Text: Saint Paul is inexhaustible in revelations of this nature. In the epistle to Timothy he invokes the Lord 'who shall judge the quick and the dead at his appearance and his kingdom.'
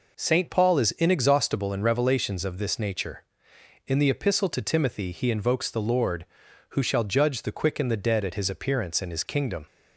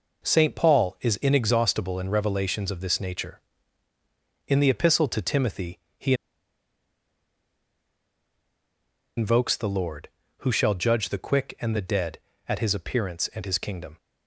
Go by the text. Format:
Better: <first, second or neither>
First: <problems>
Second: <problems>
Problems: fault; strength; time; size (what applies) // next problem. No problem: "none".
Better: first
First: none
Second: pauses between "Timothy" and "he"; slight; at 5.7 s; 0.18 s long // pauses between "he" and "invokes"; strong; at 6.1 s; 3.0 s long